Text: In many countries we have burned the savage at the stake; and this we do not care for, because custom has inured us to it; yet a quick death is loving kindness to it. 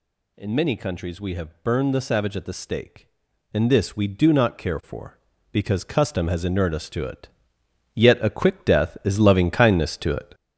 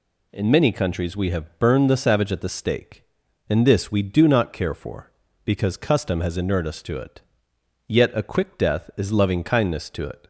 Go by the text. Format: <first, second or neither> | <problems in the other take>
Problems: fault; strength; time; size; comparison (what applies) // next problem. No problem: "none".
second | gets louder; throughout; 6.5 dB